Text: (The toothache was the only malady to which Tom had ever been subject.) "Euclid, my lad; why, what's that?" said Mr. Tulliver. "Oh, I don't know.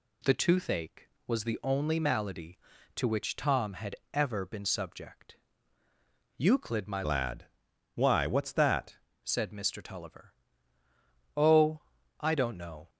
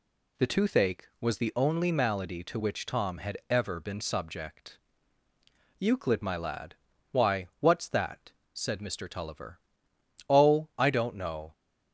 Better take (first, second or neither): second